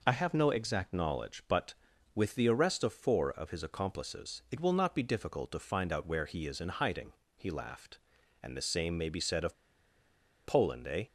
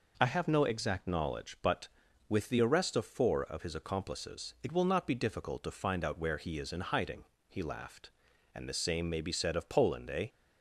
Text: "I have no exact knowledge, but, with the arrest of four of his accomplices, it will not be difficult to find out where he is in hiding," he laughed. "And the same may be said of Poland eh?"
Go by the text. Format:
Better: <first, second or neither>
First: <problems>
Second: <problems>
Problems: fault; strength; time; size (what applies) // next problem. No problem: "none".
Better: second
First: pauses between "of" and "Poland"; noticeable; at 9.5 s; 0.90 s long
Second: none